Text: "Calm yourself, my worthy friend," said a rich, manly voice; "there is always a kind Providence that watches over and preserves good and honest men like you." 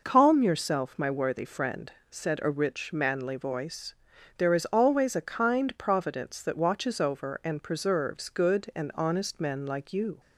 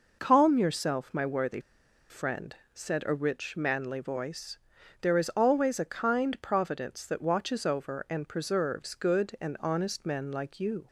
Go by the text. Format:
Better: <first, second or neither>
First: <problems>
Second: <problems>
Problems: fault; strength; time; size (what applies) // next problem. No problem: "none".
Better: first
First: none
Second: pauses between "worthy" and "friend"; noticeable; at 1.5 s; 0.51 s long